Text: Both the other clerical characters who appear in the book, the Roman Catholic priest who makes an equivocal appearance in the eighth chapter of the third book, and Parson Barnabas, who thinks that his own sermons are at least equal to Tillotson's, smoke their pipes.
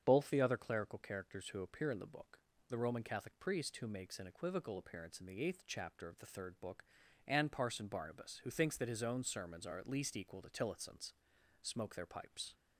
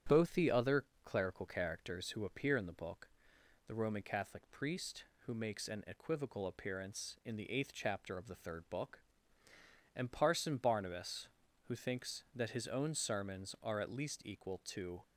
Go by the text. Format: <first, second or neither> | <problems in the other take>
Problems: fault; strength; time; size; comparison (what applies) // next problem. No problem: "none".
first | starts louder than the rest; strong; until 1.2 s; 9.5 dB; strong in the first // pauses between "other" and "clerical"; slight; at 0.8 s; 0.18 s long // stops before "Tillotson's smoke their pipes"; at 15.0 s